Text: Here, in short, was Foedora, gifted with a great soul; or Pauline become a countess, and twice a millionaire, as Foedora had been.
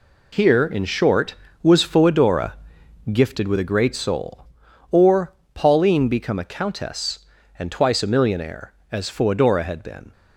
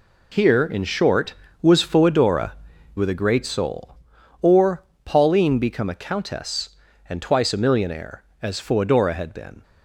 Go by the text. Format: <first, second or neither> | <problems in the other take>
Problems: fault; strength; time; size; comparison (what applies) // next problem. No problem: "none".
first | skips "gifted"; at 2.7 s // pauses between "or" and "Pauline"; slight; at 4.8 s; 0.20 s long; slight in the first